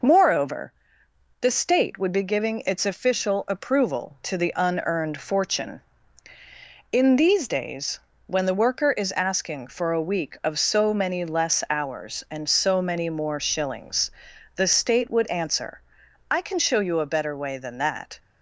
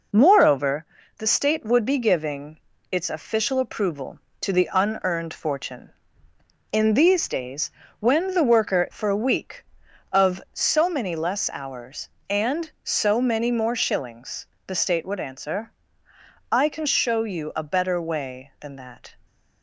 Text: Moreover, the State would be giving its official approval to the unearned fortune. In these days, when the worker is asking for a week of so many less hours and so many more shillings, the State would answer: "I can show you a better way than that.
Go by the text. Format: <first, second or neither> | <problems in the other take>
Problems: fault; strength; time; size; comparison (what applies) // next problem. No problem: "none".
first | pauses between "giving" and "its"; slight; at 2.5 s; 0.32 s long // skips "is asking"; at 8.8 s